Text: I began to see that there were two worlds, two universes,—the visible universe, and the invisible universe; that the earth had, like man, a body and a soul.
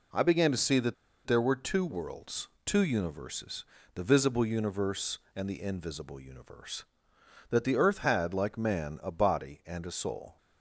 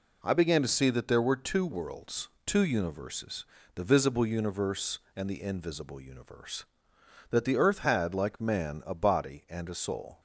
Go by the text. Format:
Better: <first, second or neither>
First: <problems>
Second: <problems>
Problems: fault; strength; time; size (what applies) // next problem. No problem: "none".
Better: second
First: pauses between "that" and "there"; slight; at 0.9 s; 0.32 s long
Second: none